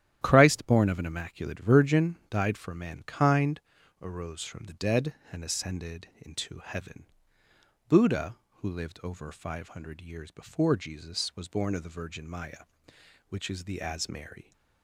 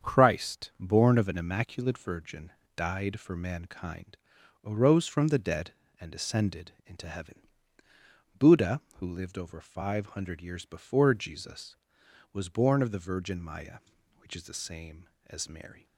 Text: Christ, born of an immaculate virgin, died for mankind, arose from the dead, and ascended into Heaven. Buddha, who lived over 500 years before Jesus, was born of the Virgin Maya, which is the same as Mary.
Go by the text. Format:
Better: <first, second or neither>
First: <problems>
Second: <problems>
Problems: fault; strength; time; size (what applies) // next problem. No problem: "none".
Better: second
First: starts louder than the rest; strong; until 1.2 s; 11.5 dB // pauses between "ascended" and "into"; slight; at 6.0 s; 0.18 s long // skips "same"; at 13.8 s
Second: starts louder than the rest; strong; until 1.1 s; 7.5 dB